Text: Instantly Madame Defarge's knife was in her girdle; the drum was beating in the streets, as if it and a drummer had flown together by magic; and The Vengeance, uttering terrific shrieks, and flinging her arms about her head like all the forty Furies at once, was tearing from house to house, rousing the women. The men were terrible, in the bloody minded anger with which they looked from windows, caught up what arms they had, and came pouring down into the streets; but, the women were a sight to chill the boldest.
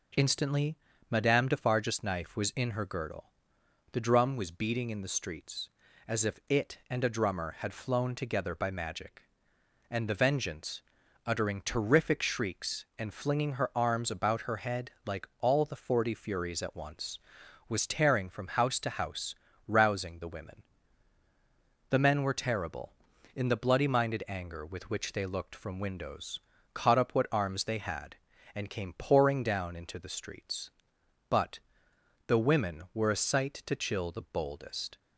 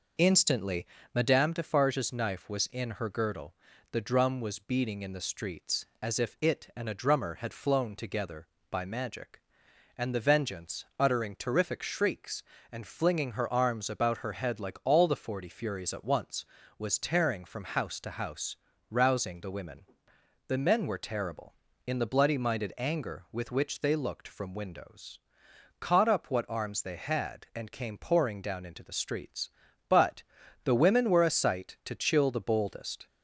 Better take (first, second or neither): first